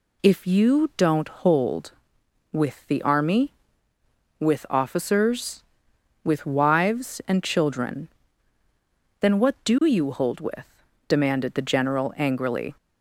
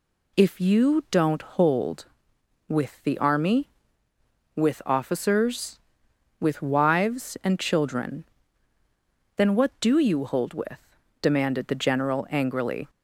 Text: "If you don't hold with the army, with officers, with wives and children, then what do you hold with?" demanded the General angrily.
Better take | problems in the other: neither | none

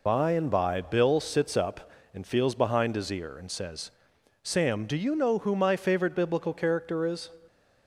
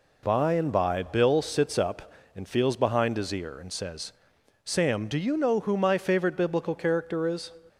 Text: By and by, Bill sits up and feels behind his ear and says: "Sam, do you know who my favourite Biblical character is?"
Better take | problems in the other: second | loses the start of "By"; at 0.0 s; 45 ms

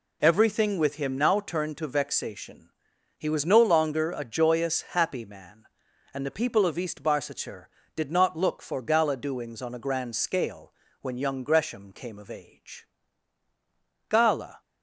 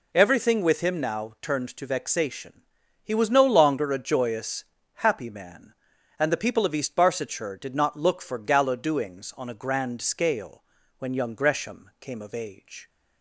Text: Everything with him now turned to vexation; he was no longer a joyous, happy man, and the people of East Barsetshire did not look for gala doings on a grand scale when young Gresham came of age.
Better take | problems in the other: second | pauses between "scale" and "when"; slight; at 10.7 s; 0.26 s long; slight in the second // goes on to say "Gala"; from 14.1 s on; 0.50 s long

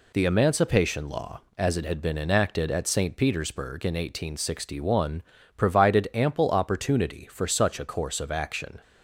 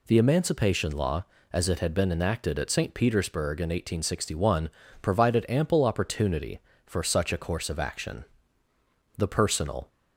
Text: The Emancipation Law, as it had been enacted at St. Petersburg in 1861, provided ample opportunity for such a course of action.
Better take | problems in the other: first | goes on to say "The personal"; noticeable; from 9.1 s on; 0.72 s long

